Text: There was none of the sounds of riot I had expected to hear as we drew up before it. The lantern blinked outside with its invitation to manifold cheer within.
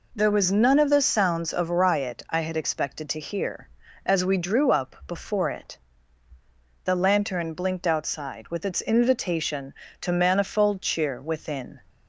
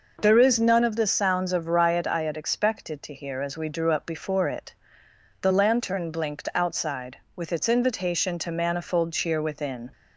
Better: first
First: none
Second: says "is" for "was"; at 0.3 s

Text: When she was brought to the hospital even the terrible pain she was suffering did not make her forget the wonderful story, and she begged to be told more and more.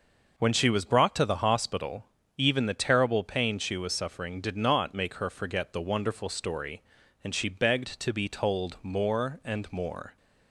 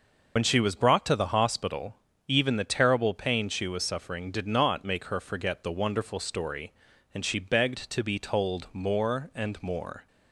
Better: first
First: pauses between "hospital" and "even"; slight; at 2.0 s; 0.32 s long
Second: loses the start of "When"; at 0.3 s; 70 ms // pauses between "hospital" and "even"; slight; at 1.9 s; 0.32 s long

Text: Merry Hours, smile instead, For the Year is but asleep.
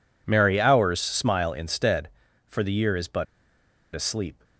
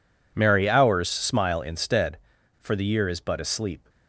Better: second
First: pauses between "but" and "asleep"; noticeable; at 3.2 s; 0.70 s long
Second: none

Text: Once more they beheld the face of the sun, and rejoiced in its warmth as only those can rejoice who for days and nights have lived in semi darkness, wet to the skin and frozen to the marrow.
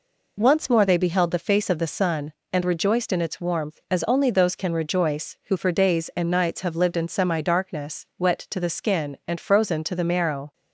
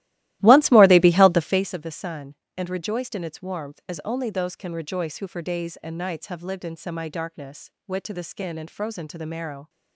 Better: first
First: none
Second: starts louder than the rest; strong; until 1.8 s; 16 dB

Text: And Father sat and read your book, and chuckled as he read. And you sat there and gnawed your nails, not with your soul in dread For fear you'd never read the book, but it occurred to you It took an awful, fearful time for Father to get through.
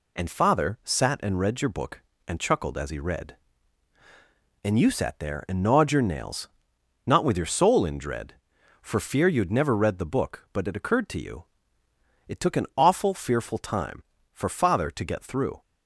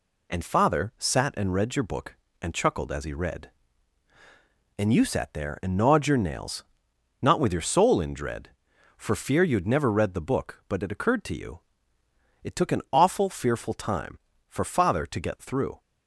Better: neither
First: pauses between "you" and "It"; noticeable; at 11.4 s; 0.82 s long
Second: pauses between "you" and "It"; noticeable; at 11.6 s; 0.82 s long

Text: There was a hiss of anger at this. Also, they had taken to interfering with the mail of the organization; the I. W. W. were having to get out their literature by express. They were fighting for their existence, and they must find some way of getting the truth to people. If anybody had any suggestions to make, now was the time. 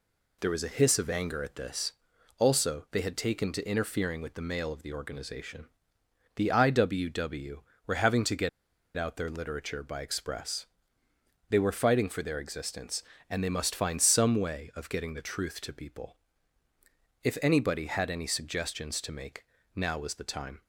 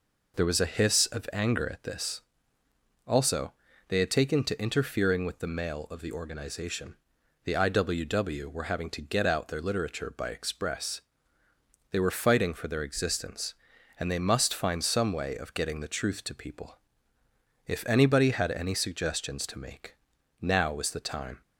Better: second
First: pauses between "get" and "out"; noticeable; at 8.4 s; 0.48 s long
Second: none

